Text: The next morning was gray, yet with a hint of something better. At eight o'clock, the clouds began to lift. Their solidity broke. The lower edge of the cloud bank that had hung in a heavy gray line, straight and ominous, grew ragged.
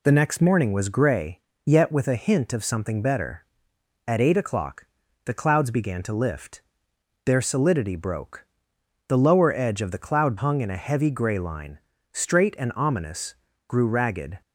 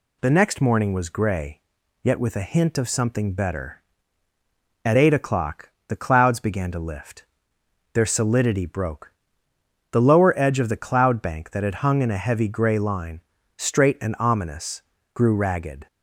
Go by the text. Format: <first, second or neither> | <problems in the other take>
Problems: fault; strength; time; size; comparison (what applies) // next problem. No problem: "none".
second | skips "bank that had"; at 10.3 s